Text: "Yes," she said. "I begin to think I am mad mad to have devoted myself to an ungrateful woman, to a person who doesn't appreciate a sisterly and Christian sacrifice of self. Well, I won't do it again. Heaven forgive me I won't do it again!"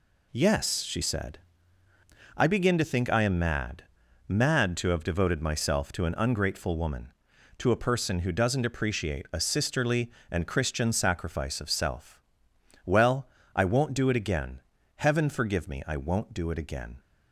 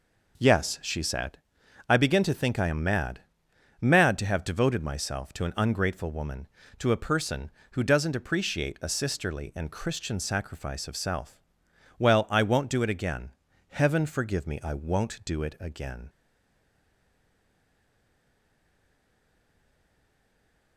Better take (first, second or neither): first